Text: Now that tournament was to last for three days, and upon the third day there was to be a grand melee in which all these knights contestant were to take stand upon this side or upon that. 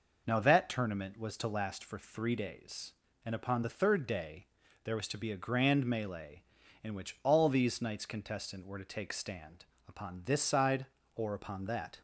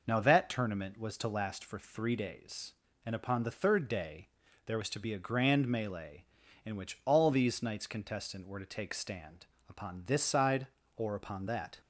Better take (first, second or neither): neither